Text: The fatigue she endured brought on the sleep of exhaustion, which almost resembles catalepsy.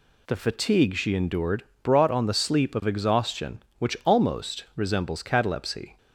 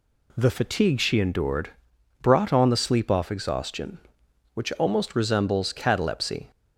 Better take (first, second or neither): first